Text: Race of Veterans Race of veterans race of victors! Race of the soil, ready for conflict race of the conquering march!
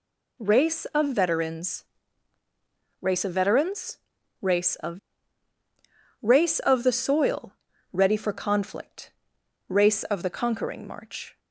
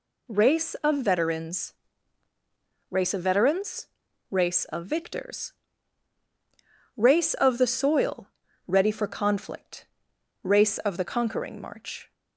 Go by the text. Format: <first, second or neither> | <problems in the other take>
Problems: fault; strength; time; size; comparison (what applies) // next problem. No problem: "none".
second | pauses between "Veterans" and "Race"; at 1.8 s; 1.1 s long; also in the second // pauses between "veterans" and "race"; at 3.9 s; 0.42 s long; also in the second // skips "victors"; at 5.5 s // pauses between "conflict" and "race"; noticeable; at 9.1 s; 0.56 s long; noticeable in the second